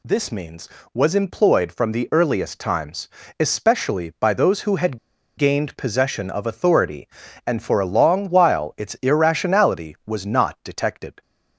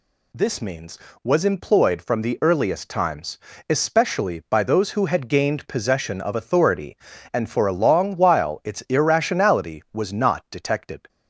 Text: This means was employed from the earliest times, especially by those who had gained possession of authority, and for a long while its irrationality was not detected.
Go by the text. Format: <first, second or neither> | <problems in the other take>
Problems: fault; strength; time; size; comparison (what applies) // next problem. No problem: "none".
second | pauses between "had" and "gained"; at 4.9 s; 0.41 s long